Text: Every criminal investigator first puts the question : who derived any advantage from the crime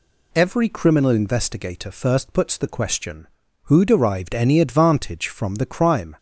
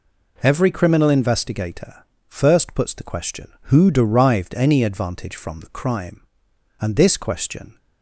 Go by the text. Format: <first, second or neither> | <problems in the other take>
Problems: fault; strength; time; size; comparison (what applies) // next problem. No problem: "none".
first | pauses between "investigator" and "first"; slight; at 2.0 s; 0.24 s long // goes on to say "And this question"; noticeable; from 6.7 s on; 1.0 s long